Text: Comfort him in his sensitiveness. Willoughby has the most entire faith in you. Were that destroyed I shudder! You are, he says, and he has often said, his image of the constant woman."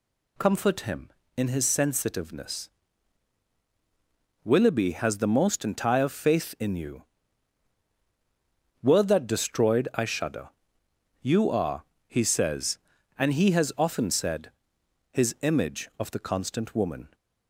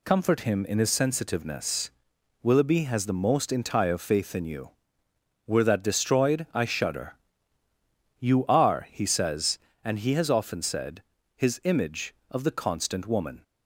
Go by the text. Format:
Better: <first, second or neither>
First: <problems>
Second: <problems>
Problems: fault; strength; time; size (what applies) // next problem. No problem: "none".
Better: neither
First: none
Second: none